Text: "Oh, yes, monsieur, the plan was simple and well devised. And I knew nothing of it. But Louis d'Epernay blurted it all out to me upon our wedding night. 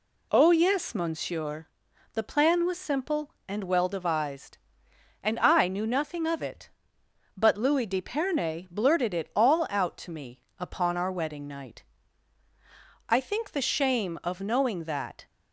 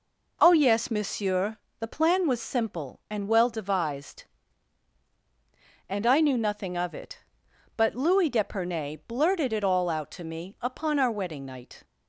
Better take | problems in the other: second | pauses between "me" and "upon"; slight; at 10.4 s; 0.18 s long // goes on to say "I think the shame of knowing that"; strong; from 13.0 s on; 2.1 s long

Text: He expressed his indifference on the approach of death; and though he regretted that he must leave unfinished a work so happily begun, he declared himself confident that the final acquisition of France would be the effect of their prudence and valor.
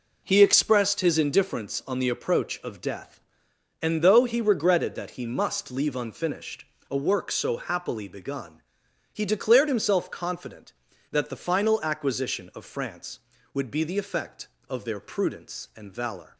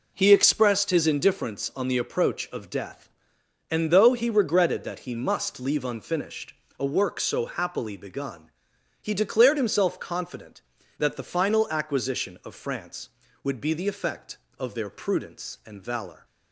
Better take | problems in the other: neither | pauses between "unfinished" and "a"; slight; the same in both

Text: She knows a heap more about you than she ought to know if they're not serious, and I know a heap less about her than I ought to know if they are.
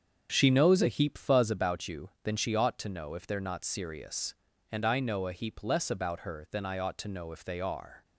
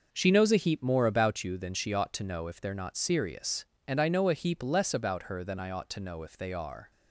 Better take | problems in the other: second | starts louder than the rest; strong; until 1.3 s; 7 dB // says "fuzz" for "more"; at 1.1 s

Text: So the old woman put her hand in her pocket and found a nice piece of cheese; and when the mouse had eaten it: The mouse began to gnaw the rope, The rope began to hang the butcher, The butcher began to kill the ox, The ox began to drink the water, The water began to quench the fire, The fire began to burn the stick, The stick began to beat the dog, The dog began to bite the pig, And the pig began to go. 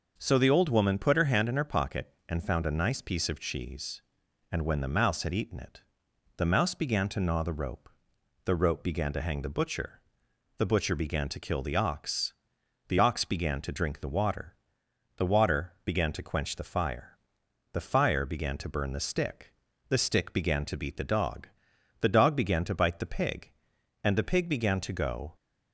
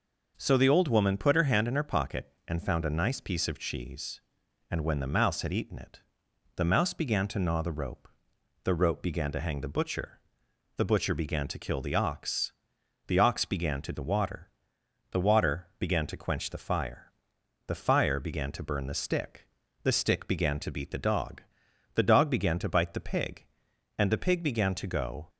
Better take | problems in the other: first | skips "drink"; at 13.9 s

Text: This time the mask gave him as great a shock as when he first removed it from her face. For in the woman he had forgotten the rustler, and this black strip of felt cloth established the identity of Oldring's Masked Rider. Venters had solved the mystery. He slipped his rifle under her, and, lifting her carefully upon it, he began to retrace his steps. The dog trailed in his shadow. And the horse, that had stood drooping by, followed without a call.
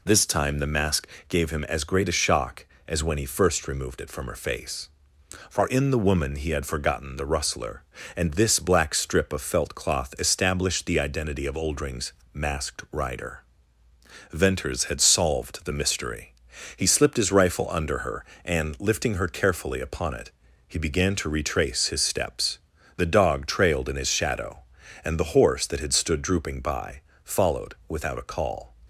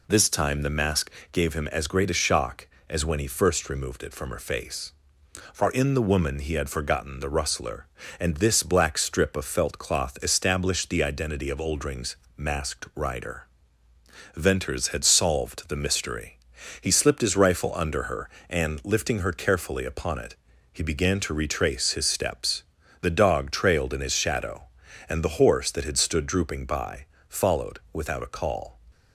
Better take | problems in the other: neither | pauses between "mask" and "gave"; slight; the same in both // pauses between "Oldring's" and "Masked"; slight; the same in both

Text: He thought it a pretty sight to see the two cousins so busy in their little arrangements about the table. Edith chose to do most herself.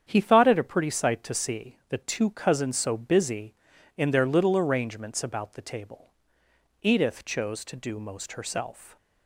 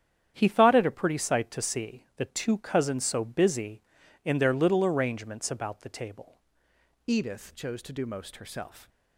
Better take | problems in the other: first | starts louder than the rest; strong; until 1.3 s; 9.5 dB; strong in the first // changes voice at "Edith"; from 7.0 s on; 1.8 s long

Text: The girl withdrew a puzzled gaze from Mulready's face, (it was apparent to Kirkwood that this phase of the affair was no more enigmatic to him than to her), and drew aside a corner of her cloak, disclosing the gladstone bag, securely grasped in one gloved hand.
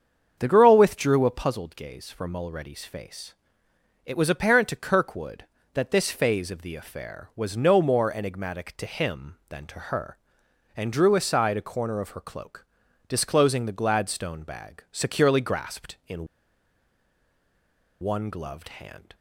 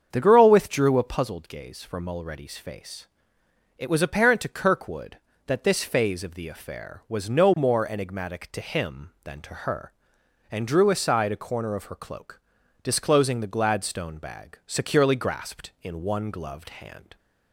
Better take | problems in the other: second | starts louder than the rest; strong; until 1.3 s; 7 dB; strong in the second // pauses between "in" and "one"; strong; at 16.2 s; 1.7 s long

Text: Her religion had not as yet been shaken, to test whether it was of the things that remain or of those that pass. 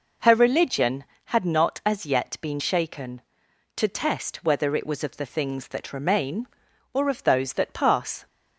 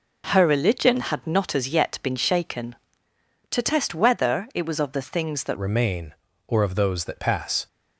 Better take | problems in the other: first | changes voice at "remain"; from 5.5 s on; 2.1 s long

